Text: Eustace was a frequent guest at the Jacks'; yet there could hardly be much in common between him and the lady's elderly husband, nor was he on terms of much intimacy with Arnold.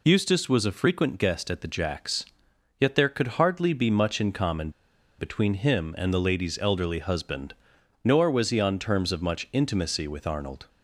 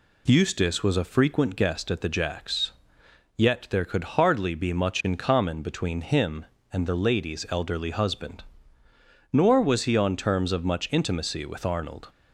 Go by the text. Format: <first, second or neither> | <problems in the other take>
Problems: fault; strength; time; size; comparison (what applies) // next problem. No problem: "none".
second | pauses between "common" and "between"; noticeable; at 4.6 s; 0.48 s long